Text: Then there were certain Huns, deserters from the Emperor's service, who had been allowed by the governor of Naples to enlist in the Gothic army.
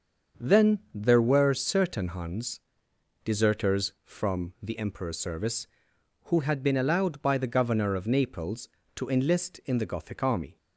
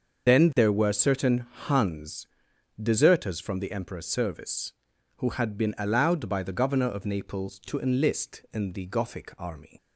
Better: first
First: starts louder than the rest; until 1.5 s; 6.5 dB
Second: loses the start of "Then"; at 0.2 s; 115 ms // starts louder than the rest; until 1.3 s; 6.5 dB // pauses between "certain" and "Huns"; slight; at 1.4 s; 0.22 s long

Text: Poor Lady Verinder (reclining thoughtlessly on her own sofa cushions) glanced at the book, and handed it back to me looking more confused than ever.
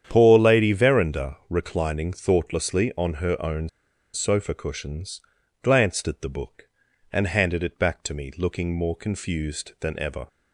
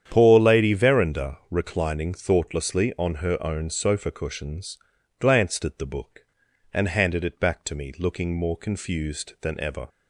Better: second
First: starts louder than the rest; strong; until 1.0 s; 9 dB // pauses between "own" and "sofa"; noticeable; at 3.6 s; 0.46 s long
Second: starts louder than the rest; strong; until 1.0 s; 9 dB

